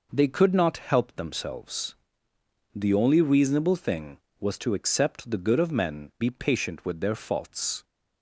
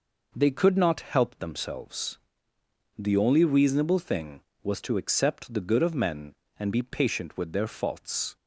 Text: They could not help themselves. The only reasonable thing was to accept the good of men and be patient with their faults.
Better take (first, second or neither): second